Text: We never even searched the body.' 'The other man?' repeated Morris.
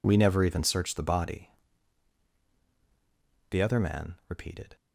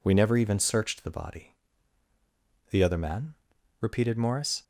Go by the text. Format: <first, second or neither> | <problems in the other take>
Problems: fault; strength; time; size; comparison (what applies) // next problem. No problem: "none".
second | stops before "Morris"; at 4.7 s